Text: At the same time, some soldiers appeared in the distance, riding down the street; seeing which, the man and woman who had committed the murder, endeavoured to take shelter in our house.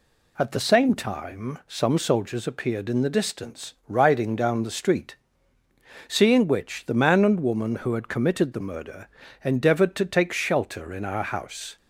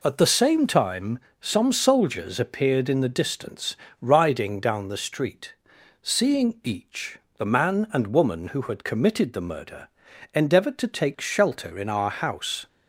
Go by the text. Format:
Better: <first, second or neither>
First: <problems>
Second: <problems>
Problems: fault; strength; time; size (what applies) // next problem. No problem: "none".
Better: first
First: none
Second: says "each" for "which"; at 6.6 s